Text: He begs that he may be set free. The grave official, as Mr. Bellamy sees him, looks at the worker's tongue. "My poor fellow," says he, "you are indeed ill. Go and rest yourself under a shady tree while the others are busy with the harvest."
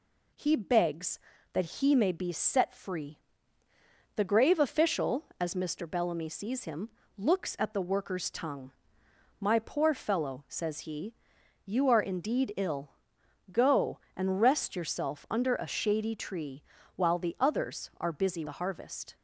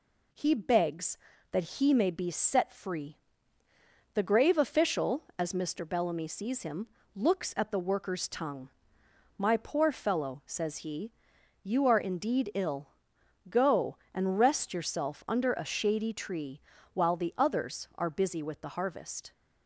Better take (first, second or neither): second